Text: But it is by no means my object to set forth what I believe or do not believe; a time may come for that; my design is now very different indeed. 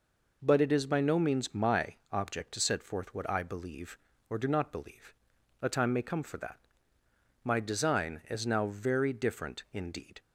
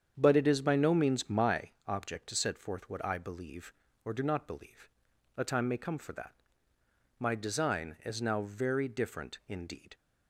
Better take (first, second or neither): first